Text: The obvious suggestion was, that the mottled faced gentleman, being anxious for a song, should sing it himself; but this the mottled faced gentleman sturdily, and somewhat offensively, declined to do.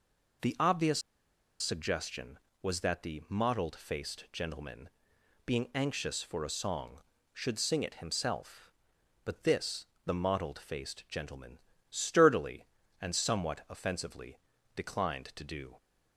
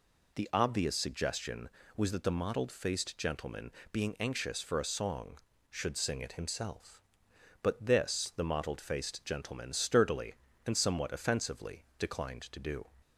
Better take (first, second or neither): second